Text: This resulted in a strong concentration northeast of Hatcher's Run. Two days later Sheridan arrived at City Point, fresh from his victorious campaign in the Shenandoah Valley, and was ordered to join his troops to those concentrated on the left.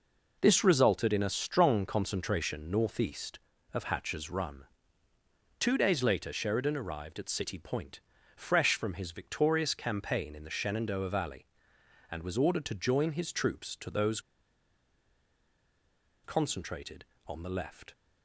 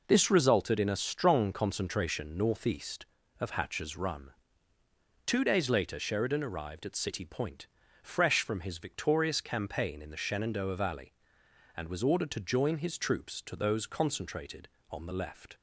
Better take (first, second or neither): second